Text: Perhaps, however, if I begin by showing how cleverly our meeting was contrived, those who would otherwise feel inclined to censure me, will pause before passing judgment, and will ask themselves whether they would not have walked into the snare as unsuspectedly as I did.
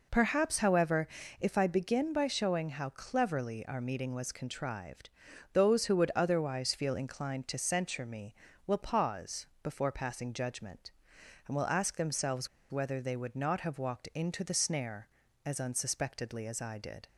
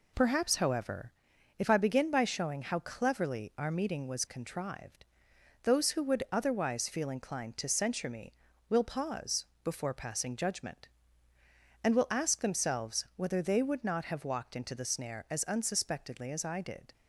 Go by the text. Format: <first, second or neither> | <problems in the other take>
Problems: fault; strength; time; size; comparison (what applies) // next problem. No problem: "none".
second | pauses between "pause" and "before"; slight; at 9.4 s; 0.16 s long; slight in the second // pauses between "themselves" and "whether"; slight; at 12.4 s; 0.23 s long